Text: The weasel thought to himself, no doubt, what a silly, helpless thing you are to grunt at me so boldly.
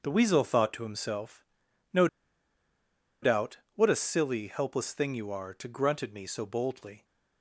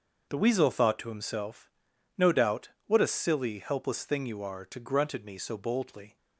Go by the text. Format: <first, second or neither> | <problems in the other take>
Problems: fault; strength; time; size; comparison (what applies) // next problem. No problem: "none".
second | starts louder than the rest; until 1.0 s; 6.5 dB; also in the second // pauses between "no" and "doubt"; at 2.0 s; 1.1 s long